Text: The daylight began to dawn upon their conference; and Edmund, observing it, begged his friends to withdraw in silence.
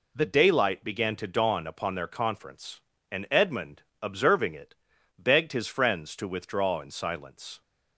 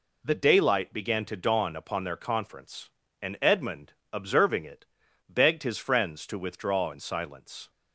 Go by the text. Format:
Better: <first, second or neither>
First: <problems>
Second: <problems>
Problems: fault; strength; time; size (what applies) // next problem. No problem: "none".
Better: neither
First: none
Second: none